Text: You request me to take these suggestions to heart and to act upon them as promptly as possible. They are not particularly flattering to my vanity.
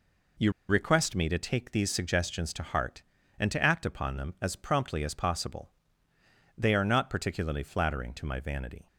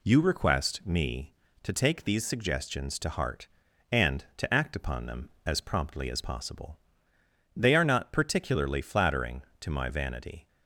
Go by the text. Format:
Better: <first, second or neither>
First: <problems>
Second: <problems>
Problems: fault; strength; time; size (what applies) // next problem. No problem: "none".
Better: second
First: pauses between "You" and "request"; slight; at 0.5 s; 0.16 s long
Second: none